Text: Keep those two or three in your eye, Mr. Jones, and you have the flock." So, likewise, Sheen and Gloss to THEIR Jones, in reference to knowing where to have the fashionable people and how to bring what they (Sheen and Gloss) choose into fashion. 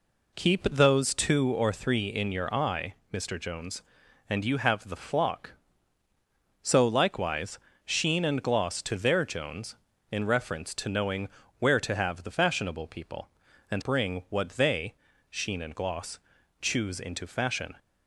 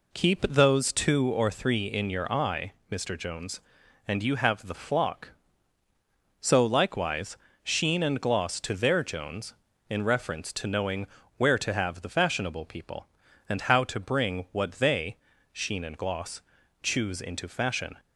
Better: second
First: pauses between "knowing" and "where"; slight; at 11.2 s; 0.30 s long // skips "how to"; at 13.8 s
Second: pauses between "knowing" and "where"; slight; at 11.0 s; 0.30 s long

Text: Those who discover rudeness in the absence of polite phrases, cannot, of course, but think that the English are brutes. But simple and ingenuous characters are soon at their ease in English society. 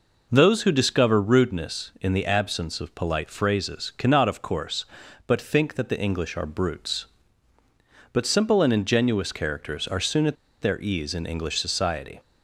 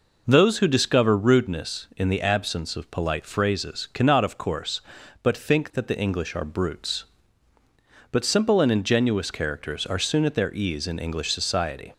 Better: second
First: pauses between "at" and "their"; slight; at 10.3 s; 0.26 s long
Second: none

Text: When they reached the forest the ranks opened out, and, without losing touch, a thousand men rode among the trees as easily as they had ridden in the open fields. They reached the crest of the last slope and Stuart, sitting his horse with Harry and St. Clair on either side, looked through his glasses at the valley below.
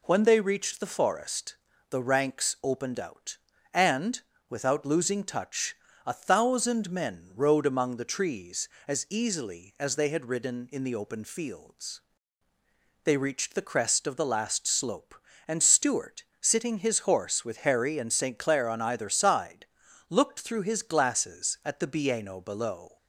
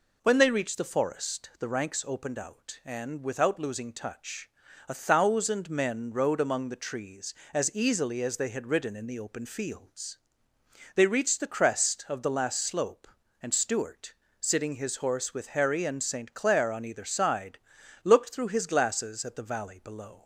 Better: second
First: pauses between "forest" and "the"; slight; at 1.5 s; 0.34 s long // says "bieno" for "valley"; at 21.8 s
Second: none

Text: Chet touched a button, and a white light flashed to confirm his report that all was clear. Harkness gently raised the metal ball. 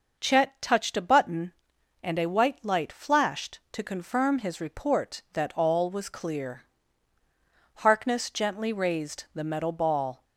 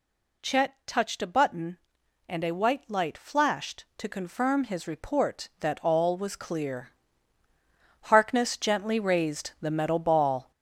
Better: first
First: none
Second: gets louder; throughout; 7 dB

